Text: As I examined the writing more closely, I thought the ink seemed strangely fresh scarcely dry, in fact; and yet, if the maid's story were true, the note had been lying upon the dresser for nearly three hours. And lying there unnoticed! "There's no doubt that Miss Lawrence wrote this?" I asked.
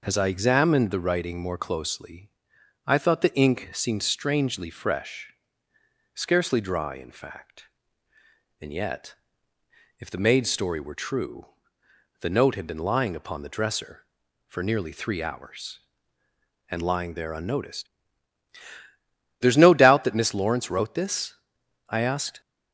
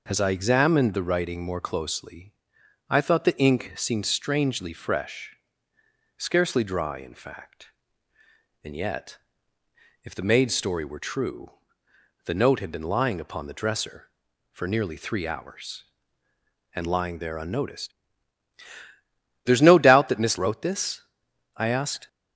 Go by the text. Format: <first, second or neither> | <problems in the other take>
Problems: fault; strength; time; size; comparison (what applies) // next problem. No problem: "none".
first | pauses between "fresh" and "scarcely"; noticeable; at 5.3 s; 0.86 s long; noticeable in the first // skips "Lawrence"; at 20.3 s